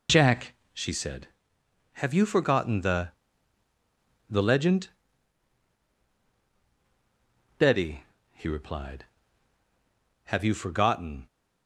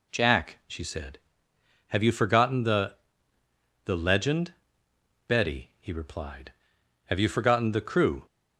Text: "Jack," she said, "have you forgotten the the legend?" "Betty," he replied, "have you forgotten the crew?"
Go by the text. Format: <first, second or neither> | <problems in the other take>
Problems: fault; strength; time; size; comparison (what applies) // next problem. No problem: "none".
second | pauses between "the" and "the"; at 3.1 s; 1.1 s long; noticeable in the second // stops before "the crew"; at 11.2 s